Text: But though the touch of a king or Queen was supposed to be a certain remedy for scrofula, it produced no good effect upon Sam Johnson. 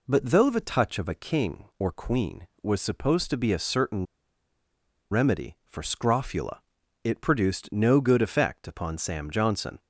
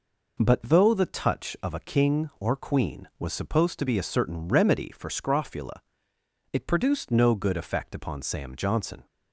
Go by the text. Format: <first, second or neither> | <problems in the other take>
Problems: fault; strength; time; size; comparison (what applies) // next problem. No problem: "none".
second | pauses between "certain" and "remedy"; at 4.0 s; 1.0 s long